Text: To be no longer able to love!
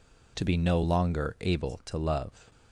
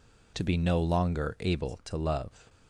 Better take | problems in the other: neither | none

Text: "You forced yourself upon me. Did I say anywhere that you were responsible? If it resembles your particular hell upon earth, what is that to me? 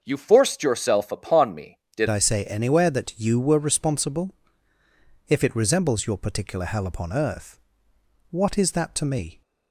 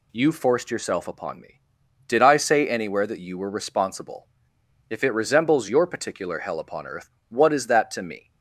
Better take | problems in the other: second | starts louder than the rest; until 1.0 s; 6.5 dB // changes voice at "I"; from 2.0 s on; 7.4 s long

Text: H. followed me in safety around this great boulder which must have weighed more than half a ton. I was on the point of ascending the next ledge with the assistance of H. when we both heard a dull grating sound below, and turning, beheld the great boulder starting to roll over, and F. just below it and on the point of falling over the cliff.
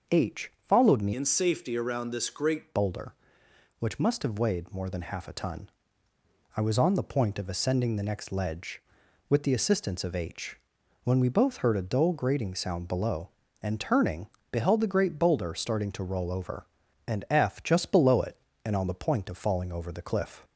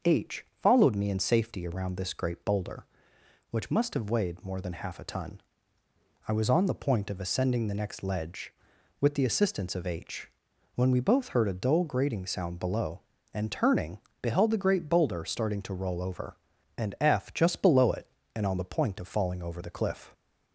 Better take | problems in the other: second | starts louder than the rest; noticeable; until 1.2 s; 6 dB; also in the second // changes voice from "in" to "great"; from 1.1 to 2.7 s; 1.6 s long

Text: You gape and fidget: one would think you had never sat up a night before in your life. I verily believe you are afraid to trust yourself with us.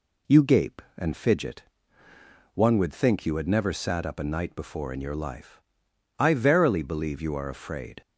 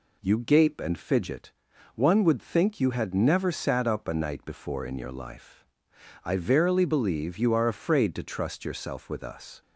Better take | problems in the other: second | stops before "to trust yourself with us"; at 8.0 s

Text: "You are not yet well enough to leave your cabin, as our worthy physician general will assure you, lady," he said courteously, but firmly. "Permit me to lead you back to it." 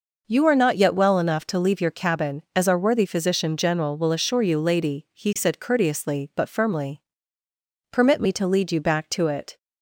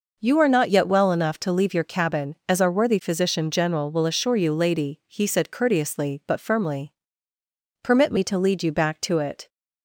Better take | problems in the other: neither | none

